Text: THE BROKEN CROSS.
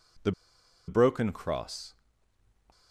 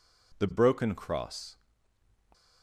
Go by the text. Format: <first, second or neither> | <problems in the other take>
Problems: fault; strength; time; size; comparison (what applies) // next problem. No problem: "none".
second | pauses between "THE" and "BROKEN"; noticeable; at 0.3 s; 0.56 s long